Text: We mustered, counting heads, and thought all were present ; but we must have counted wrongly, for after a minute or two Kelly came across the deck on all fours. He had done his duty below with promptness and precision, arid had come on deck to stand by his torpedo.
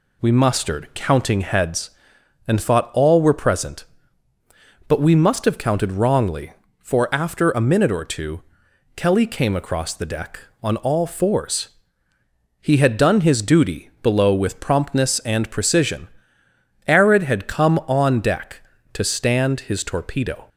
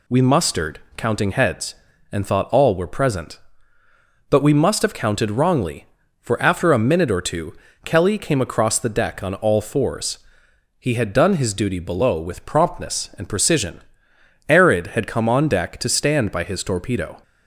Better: second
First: pauses between "two" and "Kelly"; noticeable; at 8.4 s; 0.54 s long // skips "by"; at 19.6 s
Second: pauses between "two" and "Kelly"; slight; at 7.5 s; 0.29 s long

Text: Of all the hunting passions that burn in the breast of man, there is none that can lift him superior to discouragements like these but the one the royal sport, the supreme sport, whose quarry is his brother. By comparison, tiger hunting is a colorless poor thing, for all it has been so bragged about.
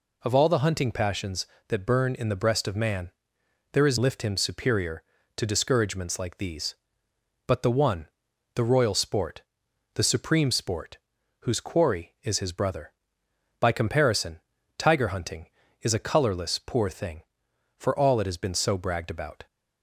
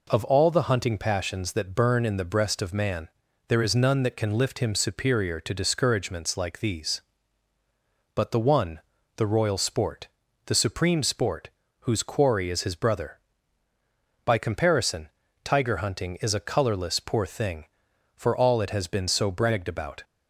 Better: second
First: skips "none that can"; at 3.9 s // pauses between "one" and "the"; noticeable; at 8.0 s; 0.48 s long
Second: pauses between "one" and "the"; slight; at 8.8 s; 0.36 s long

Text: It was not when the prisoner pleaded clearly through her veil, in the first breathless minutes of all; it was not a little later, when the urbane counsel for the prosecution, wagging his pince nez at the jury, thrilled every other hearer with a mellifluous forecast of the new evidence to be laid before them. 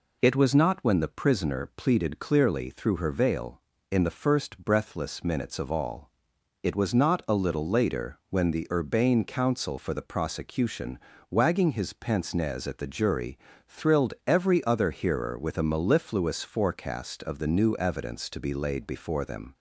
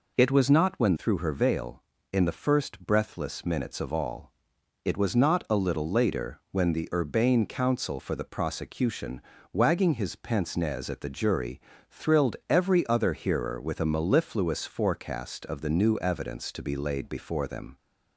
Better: first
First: none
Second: skips "the prisoner pleaded clearly"; at 0.9 s

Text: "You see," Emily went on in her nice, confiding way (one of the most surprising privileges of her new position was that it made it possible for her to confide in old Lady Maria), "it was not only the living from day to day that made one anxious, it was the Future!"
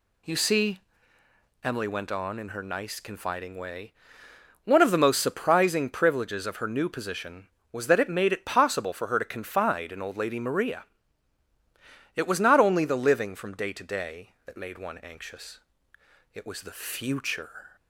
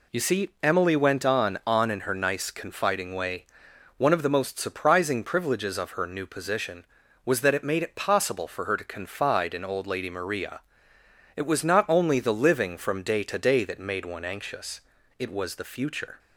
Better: first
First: none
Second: says "on" twice; at 1.6 s

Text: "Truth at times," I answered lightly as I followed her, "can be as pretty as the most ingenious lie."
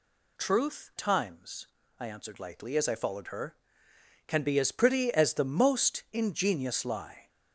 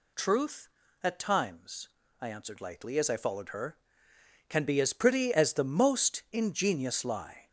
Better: second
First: skips "at"; at 0.9 s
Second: none

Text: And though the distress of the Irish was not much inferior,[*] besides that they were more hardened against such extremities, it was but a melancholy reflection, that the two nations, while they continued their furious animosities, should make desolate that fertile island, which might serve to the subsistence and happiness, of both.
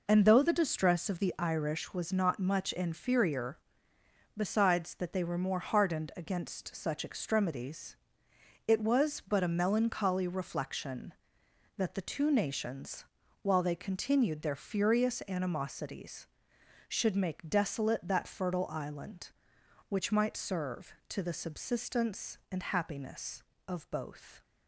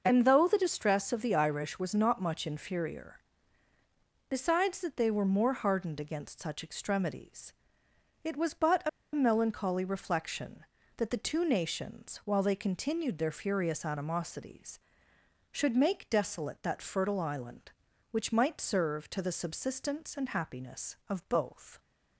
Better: first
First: none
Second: starts louder than the rest; until 1.0 s; 6 dB // pauses between "a" and "melancholy"; slight; at 8.8 s; 0.24 s long

